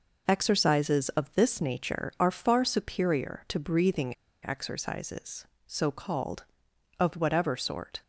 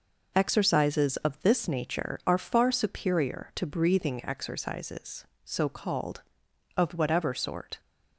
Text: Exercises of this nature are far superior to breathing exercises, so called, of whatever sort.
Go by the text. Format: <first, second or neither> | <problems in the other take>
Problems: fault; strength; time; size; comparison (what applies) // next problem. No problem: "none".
second | pauses between "breathing" and "exercises"; slight; at 4.1 s; 0.28 s long